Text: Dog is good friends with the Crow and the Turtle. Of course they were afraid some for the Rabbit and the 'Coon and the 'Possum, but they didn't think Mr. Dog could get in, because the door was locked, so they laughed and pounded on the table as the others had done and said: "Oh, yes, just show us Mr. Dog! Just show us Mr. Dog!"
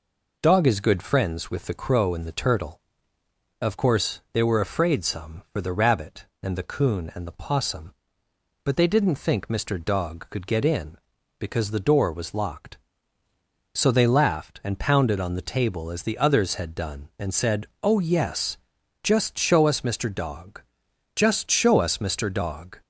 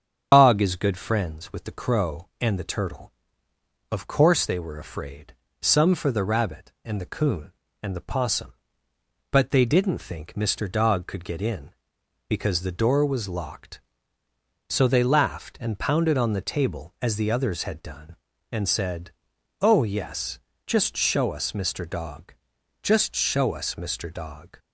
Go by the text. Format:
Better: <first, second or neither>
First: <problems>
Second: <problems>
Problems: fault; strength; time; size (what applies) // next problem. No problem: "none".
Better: first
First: none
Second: loses the start of "Dog"; at 0.3 s; 95 ms // starts louder than the rest; strong; until 1.3 s; 7.5 dB // pauses between "afraid" and "some"; slight; at 5.3 s; 0.28 s long